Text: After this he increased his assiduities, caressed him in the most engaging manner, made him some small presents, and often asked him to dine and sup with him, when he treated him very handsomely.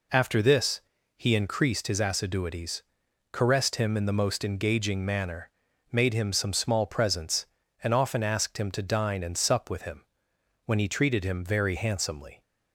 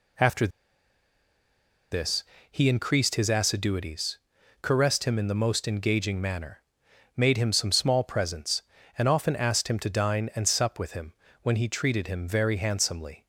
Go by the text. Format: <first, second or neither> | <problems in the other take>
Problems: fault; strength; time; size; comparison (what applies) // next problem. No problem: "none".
first | pauses between "After" and "this"; strong; at 0.4 s; 1.4 s long // pauses between "this" and "he"; slight; at 2.2 s; 0.28 s long; slight in the first